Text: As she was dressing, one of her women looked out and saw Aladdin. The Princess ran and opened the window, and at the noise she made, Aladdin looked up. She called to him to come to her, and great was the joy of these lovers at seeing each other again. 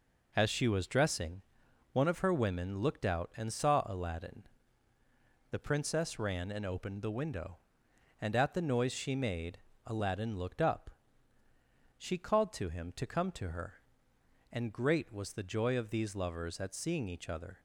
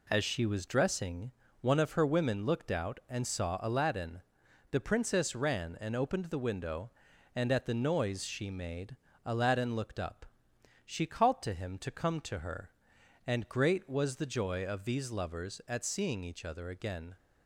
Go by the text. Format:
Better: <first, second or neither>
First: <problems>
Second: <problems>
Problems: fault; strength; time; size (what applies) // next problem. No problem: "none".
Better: second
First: stops before "again"; at 17.5 s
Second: none